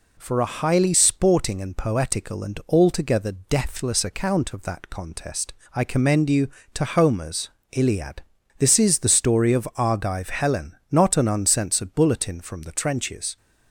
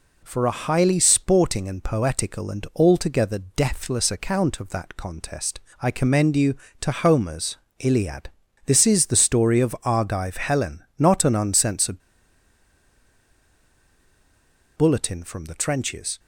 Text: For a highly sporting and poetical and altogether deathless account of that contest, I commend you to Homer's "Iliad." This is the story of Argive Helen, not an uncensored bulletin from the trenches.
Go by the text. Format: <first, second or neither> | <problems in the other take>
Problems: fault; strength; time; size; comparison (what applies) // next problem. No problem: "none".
first | pauses between "Homer's" and "Iliad"; slight; at 7.5 s; 0.22 s long; slight in the first // pauses between "uncensored" and "bulletin"; strong; at 12.0 s; 2.7 s long